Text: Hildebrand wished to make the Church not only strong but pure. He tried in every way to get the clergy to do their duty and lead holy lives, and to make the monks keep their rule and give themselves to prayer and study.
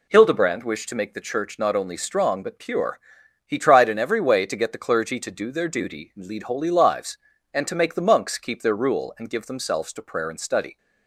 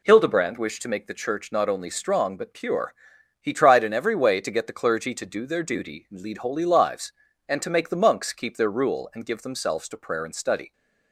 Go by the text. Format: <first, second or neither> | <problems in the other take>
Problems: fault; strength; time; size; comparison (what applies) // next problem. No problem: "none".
neither | none